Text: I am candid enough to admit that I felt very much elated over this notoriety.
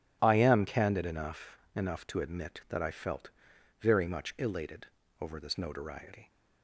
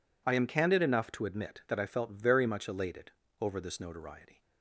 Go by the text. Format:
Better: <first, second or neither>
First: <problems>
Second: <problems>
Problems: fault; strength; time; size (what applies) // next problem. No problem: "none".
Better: second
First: says "enough" twice; at 1.7 s // pauses between "felt" and "very"; noticeable; at 3.2 s; 0.50 s long // pauses between "elated" and "over"; slight; at 4.8 s; 0.34 s long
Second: pauses between "elated" and "over"; slight; at 3.1 s; 0.30 s long